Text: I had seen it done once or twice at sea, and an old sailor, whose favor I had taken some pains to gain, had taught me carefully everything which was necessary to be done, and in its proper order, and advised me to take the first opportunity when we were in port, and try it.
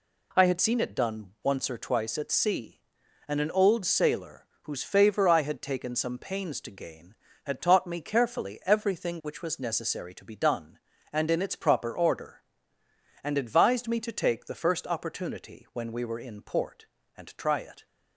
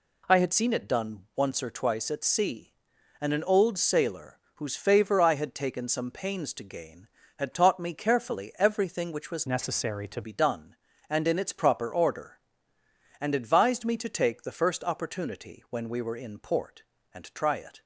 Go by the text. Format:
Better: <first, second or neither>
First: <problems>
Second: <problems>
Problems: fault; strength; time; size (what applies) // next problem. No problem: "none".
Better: first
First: none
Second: changes voice from "necessary" to "to"; from 9.4 to 10.2 s; 0.8 s long